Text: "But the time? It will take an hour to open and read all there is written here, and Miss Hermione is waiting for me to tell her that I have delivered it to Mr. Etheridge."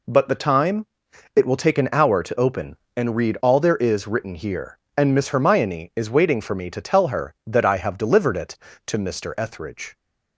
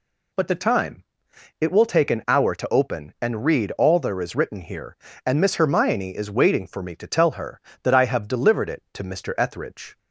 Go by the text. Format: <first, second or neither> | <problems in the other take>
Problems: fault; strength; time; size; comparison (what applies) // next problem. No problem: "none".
neither | none